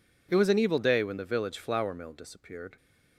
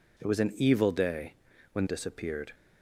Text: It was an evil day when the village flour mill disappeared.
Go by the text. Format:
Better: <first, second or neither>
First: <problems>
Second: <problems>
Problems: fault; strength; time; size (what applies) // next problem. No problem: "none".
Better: first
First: none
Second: pauses between "day" and "when"; at 1.3 s; 0.38 s long // skips "the village flour mill"; at 1.8 s